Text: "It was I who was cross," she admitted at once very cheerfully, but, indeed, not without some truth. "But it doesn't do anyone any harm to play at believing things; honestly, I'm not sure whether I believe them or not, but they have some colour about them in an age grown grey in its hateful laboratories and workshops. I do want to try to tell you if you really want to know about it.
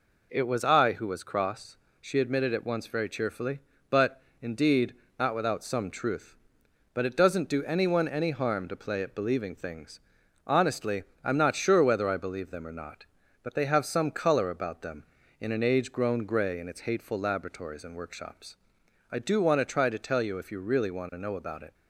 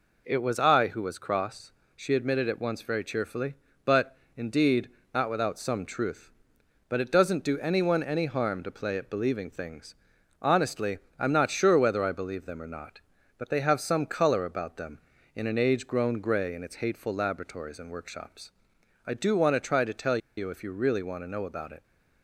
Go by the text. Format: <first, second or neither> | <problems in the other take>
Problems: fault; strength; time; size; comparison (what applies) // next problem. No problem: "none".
first | pauses between "tell" and "you"; slight; at 20.1 s; 0.19 s long